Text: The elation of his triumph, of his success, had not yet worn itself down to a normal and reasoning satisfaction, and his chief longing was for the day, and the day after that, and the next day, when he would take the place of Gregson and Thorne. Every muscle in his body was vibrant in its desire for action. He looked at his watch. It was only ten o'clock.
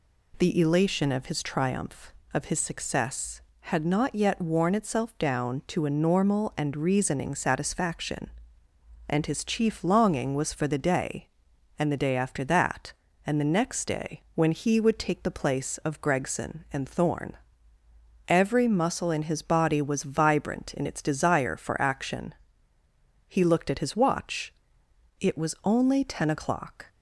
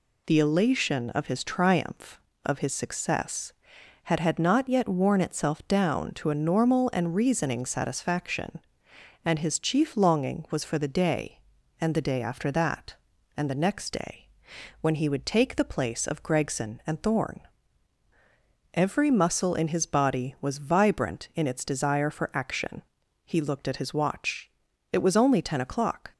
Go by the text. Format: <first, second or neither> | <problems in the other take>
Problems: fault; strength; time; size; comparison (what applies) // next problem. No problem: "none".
first | says "had" twice; at 4.2 s